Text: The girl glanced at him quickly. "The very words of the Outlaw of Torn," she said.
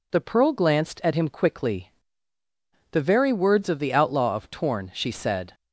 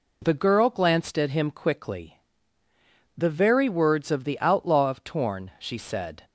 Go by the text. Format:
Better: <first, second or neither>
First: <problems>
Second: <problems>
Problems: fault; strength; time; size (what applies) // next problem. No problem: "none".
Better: second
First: says "pearl" for "girl"; at 0.2 s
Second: none